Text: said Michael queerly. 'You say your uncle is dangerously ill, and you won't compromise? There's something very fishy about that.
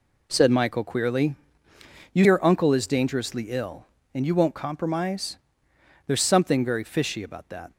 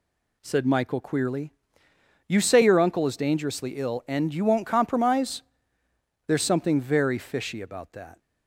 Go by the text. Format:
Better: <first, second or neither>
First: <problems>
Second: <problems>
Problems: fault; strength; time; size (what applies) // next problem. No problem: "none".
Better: second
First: skips "say"; at 2.2 s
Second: none